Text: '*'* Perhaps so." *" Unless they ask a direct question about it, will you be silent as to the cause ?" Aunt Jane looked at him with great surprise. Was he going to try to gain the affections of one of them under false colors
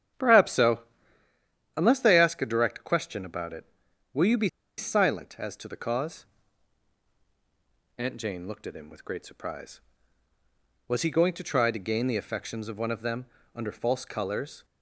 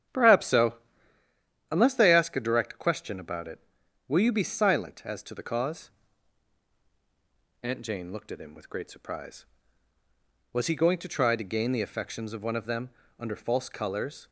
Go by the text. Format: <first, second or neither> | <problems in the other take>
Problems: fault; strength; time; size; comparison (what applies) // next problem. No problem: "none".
second | starts louder than the rest; strong; until 1.6 s; 9 dB; strong in the second // pauses between "be" and "silent"; slight; at 4.4 s; 0.31 s long // pauses between "them" and "under"; slight; at 13.2 s; 0.28 s long; slight in the second